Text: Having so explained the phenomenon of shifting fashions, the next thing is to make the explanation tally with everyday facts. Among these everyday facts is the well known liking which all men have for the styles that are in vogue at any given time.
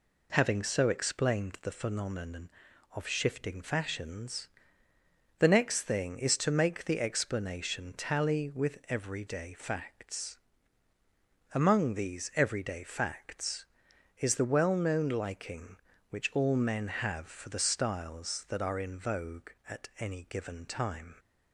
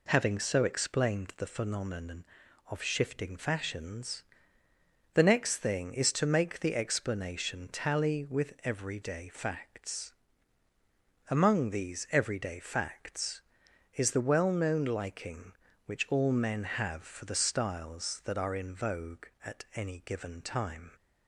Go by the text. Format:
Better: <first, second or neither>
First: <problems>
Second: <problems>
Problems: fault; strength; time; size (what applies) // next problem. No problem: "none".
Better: neither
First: none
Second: none